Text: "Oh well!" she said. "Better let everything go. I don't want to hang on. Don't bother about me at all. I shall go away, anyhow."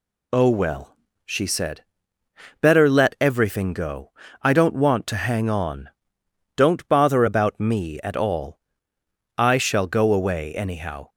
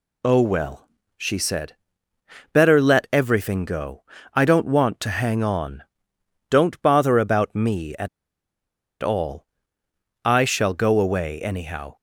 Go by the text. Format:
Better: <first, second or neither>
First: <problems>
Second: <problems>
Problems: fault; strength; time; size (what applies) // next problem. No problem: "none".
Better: first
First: none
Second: pauses between "at" and "all"; noticeable; at 8.0 s; 0.92 s long